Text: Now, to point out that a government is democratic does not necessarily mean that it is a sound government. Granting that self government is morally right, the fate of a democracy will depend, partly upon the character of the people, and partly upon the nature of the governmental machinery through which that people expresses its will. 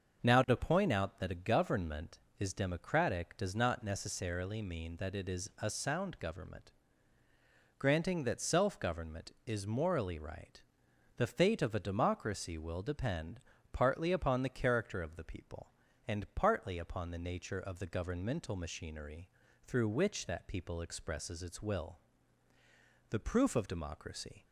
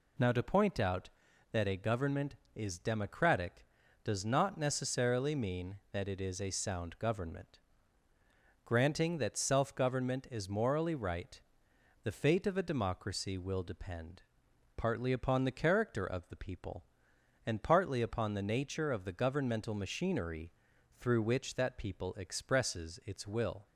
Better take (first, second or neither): second